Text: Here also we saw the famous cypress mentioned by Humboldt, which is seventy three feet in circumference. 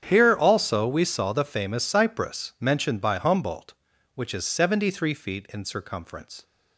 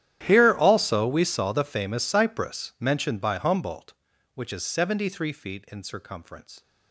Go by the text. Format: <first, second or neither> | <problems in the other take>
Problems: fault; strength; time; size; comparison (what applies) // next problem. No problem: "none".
first | gets quieter; strong; throughout; 22.5 dB // starts louder than the rest; strong; until 1.2 s; 11.5 dB; strong in the first